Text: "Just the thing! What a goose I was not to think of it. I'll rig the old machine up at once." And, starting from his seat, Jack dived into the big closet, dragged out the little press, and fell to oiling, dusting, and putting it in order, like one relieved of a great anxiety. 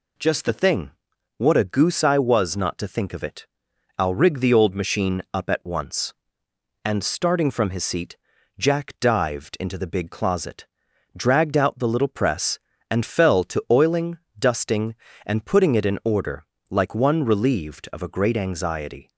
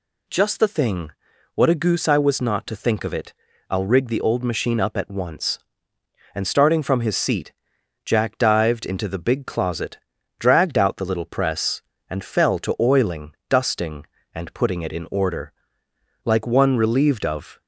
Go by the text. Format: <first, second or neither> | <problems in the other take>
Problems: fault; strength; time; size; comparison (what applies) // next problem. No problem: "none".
first | stops before "a great anxiety"; at 17.6 s